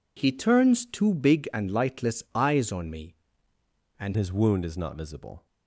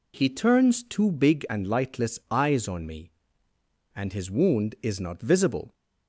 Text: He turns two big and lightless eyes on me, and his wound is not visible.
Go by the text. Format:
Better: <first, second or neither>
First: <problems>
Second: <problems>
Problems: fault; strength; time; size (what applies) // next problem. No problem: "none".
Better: second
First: changes voice at "his"; from 4.1 s on; 1.3 s long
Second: none